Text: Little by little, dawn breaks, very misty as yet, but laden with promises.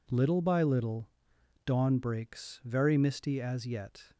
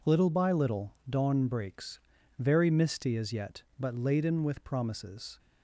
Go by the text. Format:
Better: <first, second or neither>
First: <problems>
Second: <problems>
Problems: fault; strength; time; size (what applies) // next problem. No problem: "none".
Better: second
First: stops before "but laden with promises"; at 4.1 s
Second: none